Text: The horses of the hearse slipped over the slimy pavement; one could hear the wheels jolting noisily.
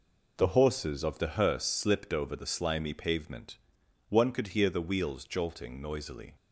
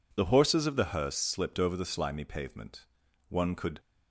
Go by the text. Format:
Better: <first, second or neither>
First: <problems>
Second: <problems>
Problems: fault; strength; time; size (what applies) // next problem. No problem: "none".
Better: first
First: none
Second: stops before "hear the wheels jolting noisily"; at 3.7 s